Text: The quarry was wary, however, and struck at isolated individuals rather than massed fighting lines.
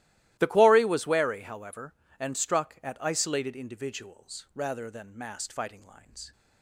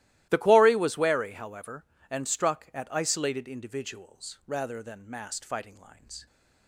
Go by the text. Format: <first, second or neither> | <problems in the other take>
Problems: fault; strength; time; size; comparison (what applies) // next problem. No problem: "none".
neither | starts louder than the rest; strong; the same in both